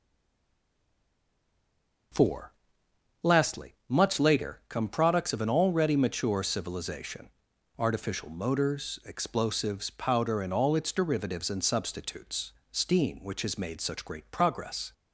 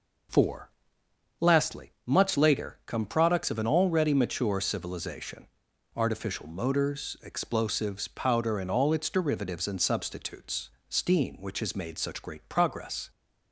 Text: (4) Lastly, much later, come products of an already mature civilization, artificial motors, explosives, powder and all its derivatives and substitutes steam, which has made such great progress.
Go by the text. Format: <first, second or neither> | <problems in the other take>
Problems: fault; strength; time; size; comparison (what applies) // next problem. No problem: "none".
second | stays silent before the first word; until 2.1 s; 2.1 s long // pauses between "substitutes" and "steam"; slight; at 12.5 s; 0.20 s long; slight in the second